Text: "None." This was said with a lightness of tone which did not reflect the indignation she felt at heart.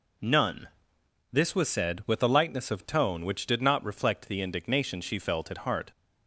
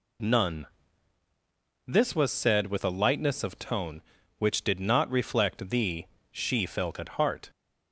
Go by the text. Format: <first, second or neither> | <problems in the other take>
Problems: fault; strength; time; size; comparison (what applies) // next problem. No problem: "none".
first | skips "indignation"; at 6.1 s